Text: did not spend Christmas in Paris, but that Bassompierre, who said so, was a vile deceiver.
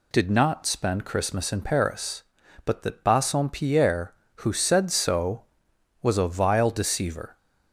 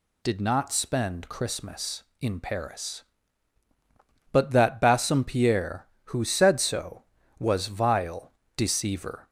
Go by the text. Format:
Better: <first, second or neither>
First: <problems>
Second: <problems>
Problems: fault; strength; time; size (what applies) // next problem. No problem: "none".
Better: first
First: none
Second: skips "a"; at 7.6 s // pauses between "vile" and "deceiver"; slight; at 8.3 s; 0.24 s long